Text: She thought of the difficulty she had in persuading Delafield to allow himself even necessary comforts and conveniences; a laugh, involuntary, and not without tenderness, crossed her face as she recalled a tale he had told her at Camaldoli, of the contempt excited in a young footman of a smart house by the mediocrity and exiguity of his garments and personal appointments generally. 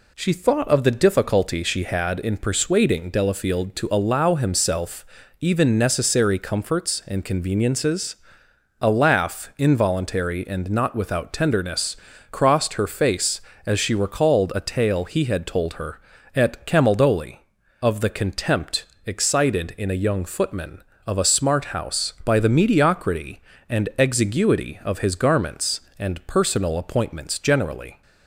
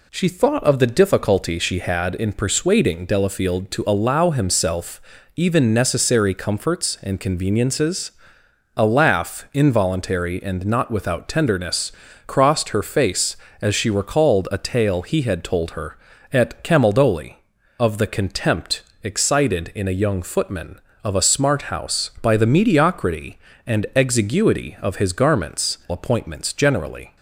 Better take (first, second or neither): first